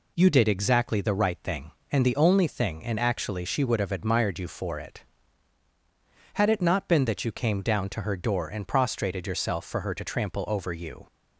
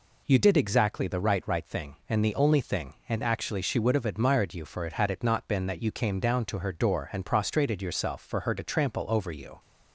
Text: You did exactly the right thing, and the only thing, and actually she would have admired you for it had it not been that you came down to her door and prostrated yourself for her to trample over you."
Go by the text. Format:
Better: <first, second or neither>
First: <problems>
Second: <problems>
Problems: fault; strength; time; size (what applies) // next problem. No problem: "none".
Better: first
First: none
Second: says "right" twice; at 1.4 s